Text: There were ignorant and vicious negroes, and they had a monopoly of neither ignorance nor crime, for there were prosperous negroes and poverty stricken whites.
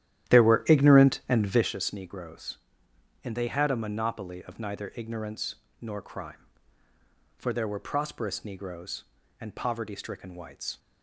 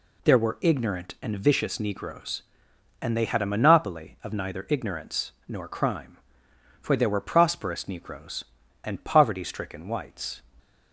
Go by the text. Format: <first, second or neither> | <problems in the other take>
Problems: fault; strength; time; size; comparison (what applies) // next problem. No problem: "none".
second | starts louder than the rest; strong; until 1.7 s; 12 dB // pauses between "ignorance" and "nor"; slight; at 5.5 s; 0.26 s long; slight in the second